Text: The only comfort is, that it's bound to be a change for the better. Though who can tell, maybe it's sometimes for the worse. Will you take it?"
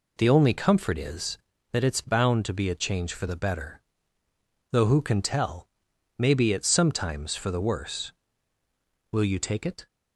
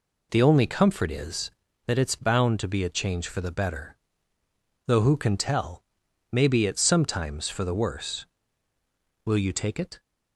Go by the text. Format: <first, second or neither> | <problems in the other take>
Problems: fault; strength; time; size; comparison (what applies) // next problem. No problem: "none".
neither | none